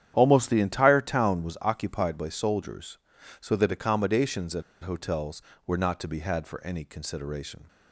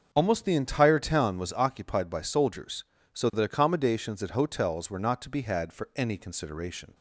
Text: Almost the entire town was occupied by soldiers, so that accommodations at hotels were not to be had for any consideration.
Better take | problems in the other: second | starts louder than the rest; strong; until 1.1 s; 10 dB; also in the second // pauses between "at" and "hotels"; slight; at 4.6 s; 0.21 s long

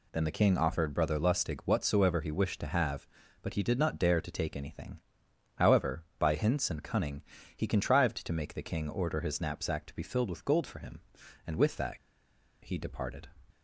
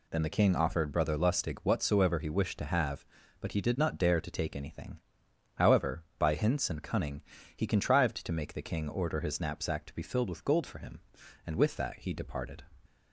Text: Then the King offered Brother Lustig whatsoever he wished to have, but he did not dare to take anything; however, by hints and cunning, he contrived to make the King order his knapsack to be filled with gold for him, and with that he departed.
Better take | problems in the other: second | pauses between "that" and "he"; noticeable; at 11.9 s; 0.64 s long

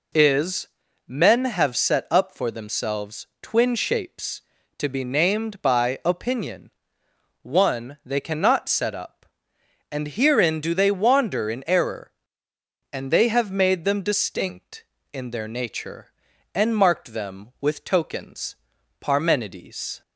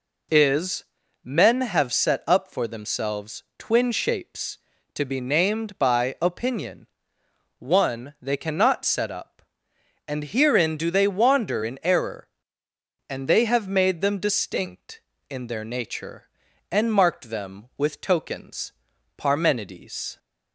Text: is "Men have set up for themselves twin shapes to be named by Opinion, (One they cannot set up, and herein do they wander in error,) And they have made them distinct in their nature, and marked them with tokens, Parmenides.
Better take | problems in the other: neither | pauses between "is" and "Men"; the same in both // pauses between "themselves" and "twin"; slight; the same in both

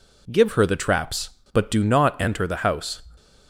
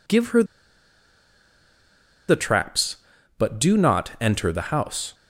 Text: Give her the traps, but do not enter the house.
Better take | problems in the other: first | pauses between "her" and "the"; strong; at 0.4 s; 1.8 s long

